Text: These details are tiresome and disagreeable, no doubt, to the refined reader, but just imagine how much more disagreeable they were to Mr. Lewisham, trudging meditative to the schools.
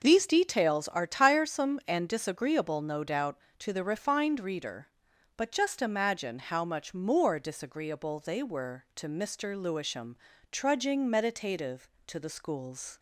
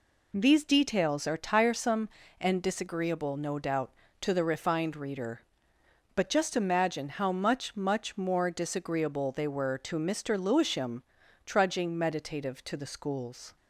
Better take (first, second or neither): first